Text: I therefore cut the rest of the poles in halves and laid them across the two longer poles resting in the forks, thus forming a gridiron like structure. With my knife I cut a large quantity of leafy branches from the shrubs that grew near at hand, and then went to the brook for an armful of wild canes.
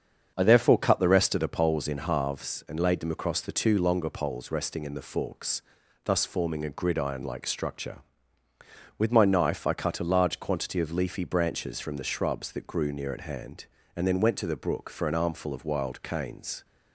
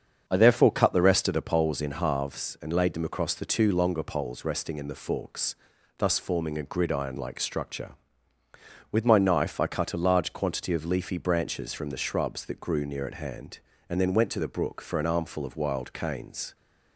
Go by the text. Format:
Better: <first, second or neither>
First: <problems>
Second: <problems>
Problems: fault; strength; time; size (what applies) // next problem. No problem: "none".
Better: neither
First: starts louder than the rest; strong; until 1.3 s; 7 dB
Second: starts louder than the rest; strong; until 1.2 s; 7 dB